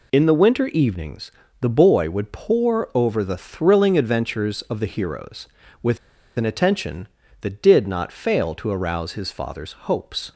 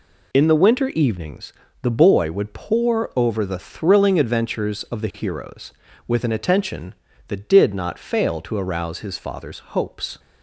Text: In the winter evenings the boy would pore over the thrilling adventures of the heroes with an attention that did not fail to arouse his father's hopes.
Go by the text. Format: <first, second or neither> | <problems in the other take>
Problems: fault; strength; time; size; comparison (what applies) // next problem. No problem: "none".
second | pauses between "evenings" and "the"; slight; at 1.2 s; 0.30 s long; slight in the second // pauses between "with" and "an"; at 5.9 s; 0.40 s long